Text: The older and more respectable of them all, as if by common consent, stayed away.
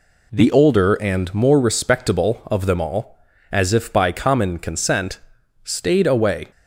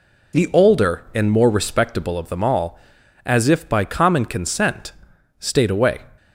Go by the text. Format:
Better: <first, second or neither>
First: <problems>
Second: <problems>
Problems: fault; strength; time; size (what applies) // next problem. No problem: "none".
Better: neither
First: none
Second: none